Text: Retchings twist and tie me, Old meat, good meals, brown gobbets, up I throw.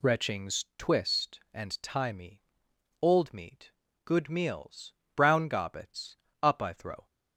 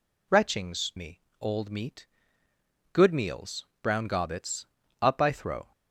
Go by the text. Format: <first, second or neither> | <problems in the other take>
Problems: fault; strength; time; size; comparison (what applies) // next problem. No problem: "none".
first | skips "twist and tie"; at 0.9 s